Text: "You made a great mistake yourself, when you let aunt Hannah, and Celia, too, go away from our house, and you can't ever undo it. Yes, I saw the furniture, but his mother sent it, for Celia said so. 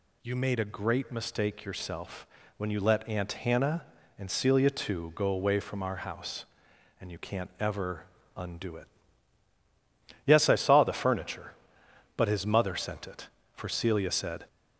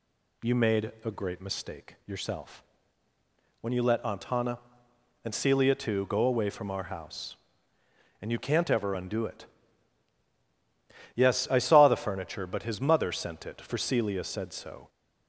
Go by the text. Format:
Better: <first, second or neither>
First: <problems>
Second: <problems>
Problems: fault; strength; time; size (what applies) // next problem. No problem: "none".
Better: second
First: pauses between "ever" and "undo"; slight; at 8.0 s; 0.30 s long // stops before "so"; at 14.4 s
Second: none